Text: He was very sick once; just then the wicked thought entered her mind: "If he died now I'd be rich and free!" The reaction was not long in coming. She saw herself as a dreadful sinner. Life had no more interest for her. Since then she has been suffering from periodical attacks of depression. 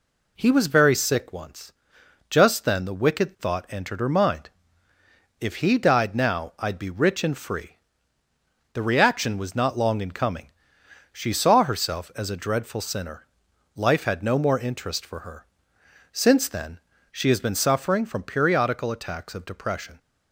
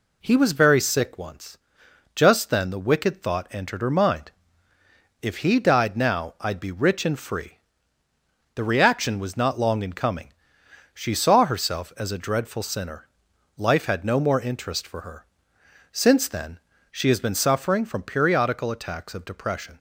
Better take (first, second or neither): neither